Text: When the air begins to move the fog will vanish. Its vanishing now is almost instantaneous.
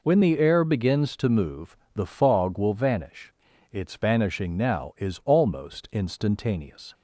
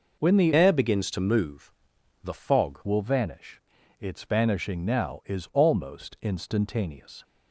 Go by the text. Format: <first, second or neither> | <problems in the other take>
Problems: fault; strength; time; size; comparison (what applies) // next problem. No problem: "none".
first | changes voice from "air" to "fog"; from 0.5 to 2.8 s; 2.3 s long // pauses between "move" and "the"; noticeable; at 1.7 s; 0.54 s long; slight in the first